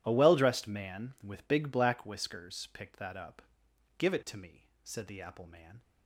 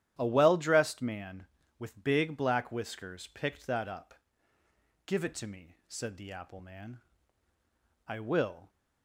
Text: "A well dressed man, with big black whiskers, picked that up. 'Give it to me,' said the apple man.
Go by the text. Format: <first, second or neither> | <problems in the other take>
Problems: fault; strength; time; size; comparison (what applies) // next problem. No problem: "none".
first | starts louder than the rest; strong; until 1.2 s; 11.5 dB // goes on to say "I will"; noticeable; from 8.0 s on; 0.62 s long